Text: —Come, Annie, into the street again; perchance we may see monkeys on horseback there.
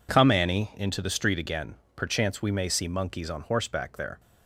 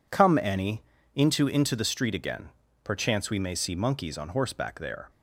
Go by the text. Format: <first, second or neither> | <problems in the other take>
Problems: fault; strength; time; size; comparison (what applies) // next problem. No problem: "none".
first | says "into" twice; at 1.4 s